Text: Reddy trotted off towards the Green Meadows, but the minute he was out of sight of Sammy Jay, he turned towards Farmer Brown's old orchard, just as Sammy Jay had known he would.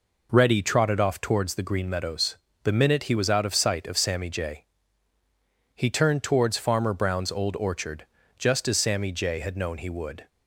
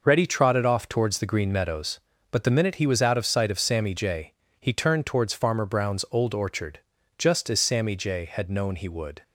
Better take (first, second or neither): second